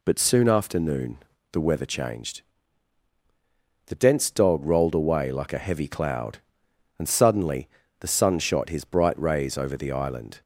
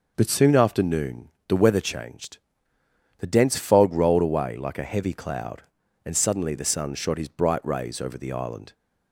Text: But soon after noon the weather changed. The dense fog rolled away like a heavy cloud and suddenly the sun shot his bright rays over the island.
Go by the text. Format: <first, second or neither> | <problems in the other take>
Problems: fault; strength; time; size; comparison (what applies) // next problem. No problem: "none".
second | pauses between "noon" and "the"; slight; at 1.1 s; 0.34 s long; slight in the second // says "dog" for "fog"; at 4.2 s // pauses between "suddenly" and "the"; slight; at 7.6 s; 0.32 s long